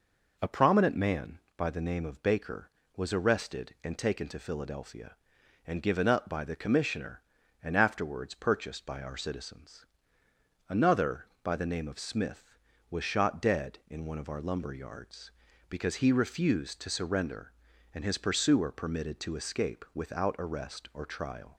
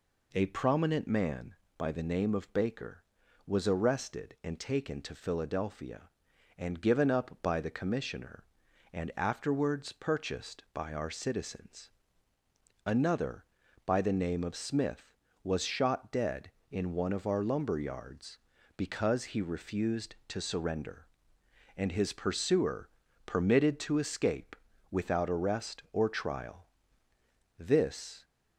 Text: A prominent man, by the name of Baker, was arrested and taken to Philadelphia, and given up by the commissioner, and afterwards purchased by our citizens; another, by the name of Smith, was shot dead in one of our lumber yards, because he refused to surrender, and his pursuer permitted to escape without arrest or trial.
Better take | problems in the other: first | pauses between "pursuer" and "permitted"; at 22.8 s; 0.38 s long // pauses between "escape" and "without"; slight; at 24.5 s; 0.34 s long // goes on to say "This"; noticeable; from 27.5 s on; 0.66 s long

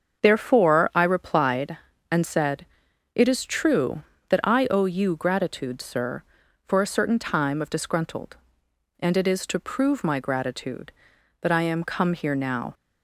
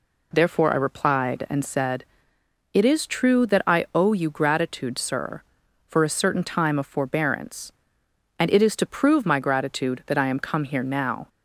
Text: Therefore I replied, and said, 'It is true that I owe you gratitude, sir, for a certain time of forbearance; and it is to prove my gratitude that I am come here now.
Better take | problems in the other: second | starts louder than the rest; until 1.2 s; 7 dB // says "disgruntled" for "forbearance"; at 7.6 s

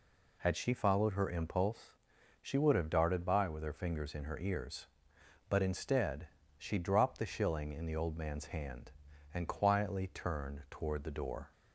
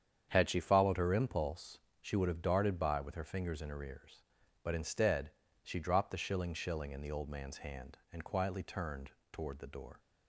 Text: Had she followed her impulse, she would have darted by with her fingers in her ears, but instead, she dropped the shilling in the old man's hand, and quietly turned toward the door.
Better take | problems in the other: first | starts louder than the rest; strong; until 1.3 s; 8 dB // says "shilling" twice; at 6.5 s // pauses between "turned" and "toward"; slight; at 9.0 s; 0.22 s long

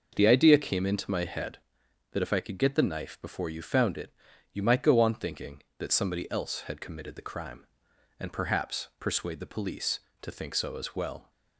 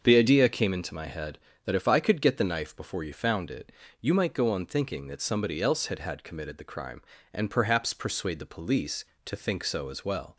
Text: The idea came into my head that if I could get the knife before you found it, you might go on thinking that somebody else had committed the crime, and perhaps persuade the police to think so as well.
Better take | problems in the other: first | starts louder than the rest; until 1.0 s; 6.5 dB // says "had" twice; at 5.9 s

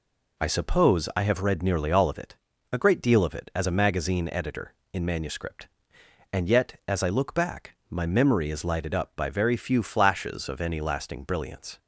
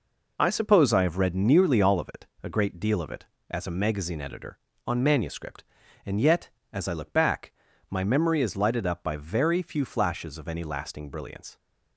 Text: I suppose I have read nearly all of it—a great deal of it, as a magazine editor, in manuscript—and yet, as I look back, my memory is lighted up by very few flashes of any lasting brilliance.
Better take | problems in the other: first | says "on" for "in"; at 4.8 s

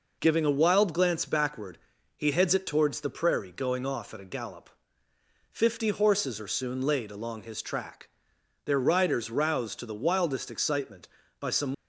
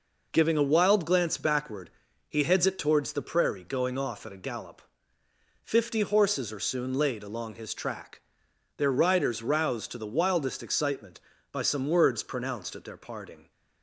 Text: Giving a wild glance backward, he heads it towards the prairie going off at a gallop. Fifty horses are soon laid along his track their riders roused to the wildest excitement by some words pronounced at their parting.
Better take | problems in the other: second | pauses between "track" and "their"; noticeable; at 8.0 s; 0.56 s long; noticeable in the second // stops before "words pronounced at their parting"; at 11.7 s

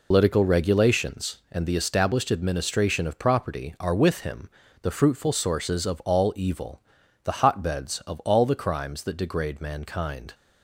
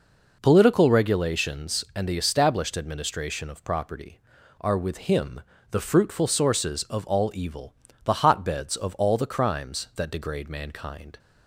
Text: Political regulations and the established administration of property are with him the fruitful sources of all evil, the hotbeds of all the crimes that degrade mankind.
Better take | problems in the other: second | loses the start of "Political"; at 0.1 s; 120 ms // pauses between "him" and "the"; slight; at 4.4 s; 0.34 s long; slight in the second

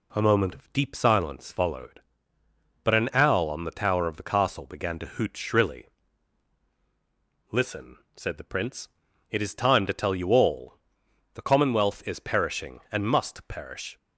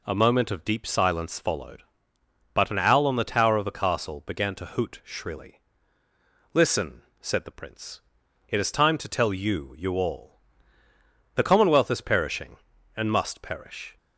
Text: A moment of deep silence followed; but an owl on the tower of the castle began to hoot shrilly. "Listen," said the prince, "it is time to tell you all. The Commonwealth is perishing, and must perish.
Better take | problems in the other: first | says "you" twice; at 9.7 s

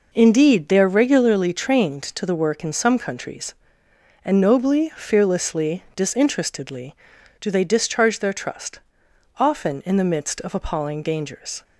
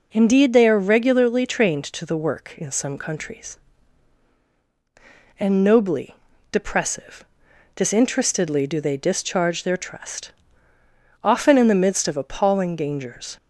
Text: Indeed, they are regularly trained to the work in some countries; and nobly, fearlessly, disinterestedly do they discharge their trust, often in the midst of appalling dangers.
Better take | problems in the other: first | says "depressive" for "fearlessly"; at 6.5 s

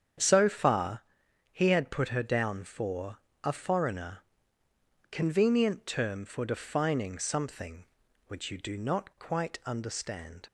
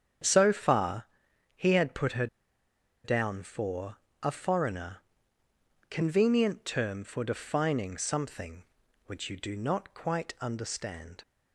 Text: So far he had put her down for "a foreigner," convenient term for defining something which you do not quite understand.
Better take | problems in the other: first | starts louder than the rest; strong; until 1.7 s; 8 dB; strong in the first // pauses between "far" and "he"; noticeable; at 1.0 s; 0.50 s long; noticeable in the first // pauses between "her" and "down"; noticeable; at 2.2 s; 0.77 s long // pauses between "for" and "a"; slight; at 3.9 s; 0.26 s long; slight in the first

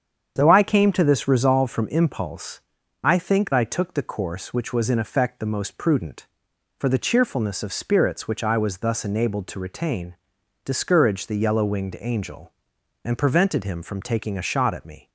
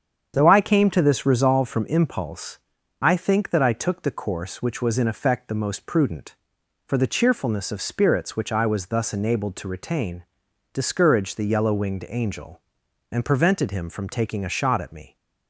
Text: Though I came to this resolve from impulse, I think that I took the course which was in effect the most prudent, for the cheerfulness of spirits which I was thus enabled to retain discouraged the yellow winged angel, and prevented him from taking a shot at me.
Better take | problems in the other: second | starts louder than the rest; strong; until 1.3 s; 8 dB; strong in the second // skips "that"; at 3.5 s // pauses between "retain" and "discouraged"; noticeable; at 10.1 s; 0.48 s long; noticeable in the second

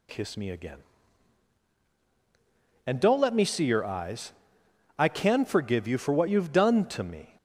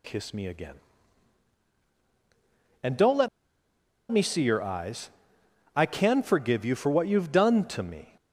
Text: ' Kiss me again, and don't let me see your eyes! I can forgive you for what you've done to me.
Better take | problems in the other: first | pauses between "let" and "me"; noticeable; at 3.2 s; 0.83 s long

